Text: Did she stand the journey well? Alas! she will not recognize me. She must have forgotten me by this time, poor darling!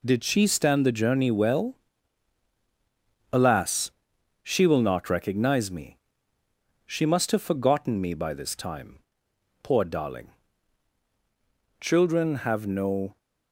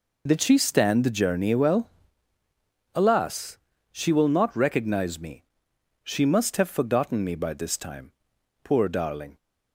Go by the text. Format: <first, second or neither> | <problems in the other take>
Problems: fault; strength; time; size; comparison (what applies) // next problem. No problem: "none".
second | goes on to say "Children have no"; from 11.8 s on; 1.3 s long